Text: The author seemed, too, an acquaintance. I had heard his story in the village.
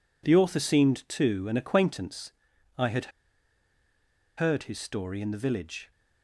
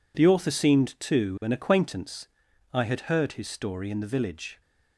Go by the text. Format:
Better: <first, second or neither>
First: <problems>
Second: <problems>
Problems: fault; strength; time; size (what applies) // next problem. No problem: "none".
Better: second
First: pauses between "had" and "heard"; strong; at 3.1 s; 1.2 s long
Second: none